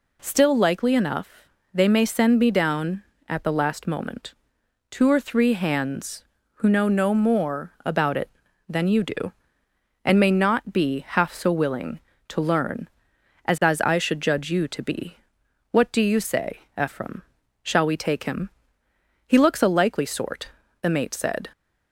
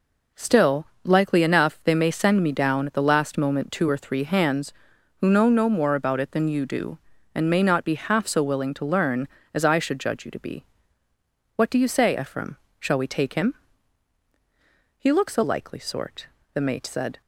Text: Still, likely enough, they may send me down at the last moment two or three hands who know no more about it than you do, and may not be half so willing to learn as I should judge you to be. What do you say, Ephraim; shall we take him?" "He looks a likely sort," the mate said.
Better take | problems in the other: second | pauses between "moment" and "two"; noticeable; at 4.3 s; 0.56 s long // says "as" twice; at 13.6 s

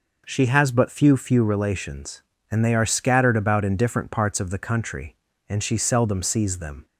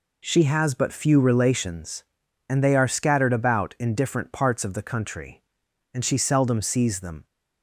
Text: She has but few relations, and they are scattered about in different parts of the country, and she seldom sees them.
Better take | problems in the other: second | says "few" twice; at 1.1 s

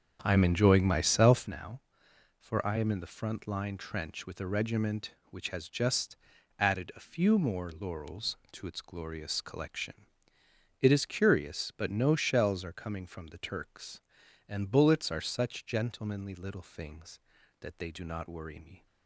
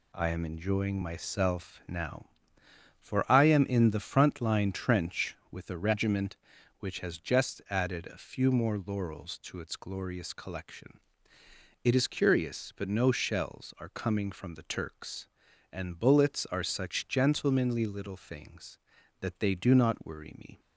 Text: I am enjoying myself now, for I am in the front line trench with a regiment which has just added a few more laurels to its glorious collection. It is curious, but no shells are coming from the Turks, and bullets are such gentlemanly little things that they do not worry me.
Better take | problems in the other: second | starts louder than the rest; strong; until 1.6 s; 7.5 dB // pauses between "just" and "added"; at 6.1 s; 0.42 s long

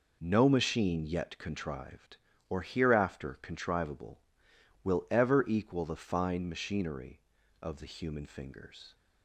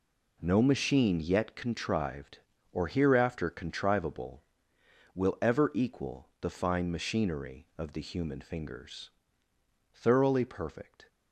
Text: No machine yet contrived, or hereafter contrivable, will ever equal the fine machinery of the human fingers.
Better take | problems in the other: first | goes on to say "Thoroughly perfect"; noticeable; from 9.9 s on; 1.1 s long

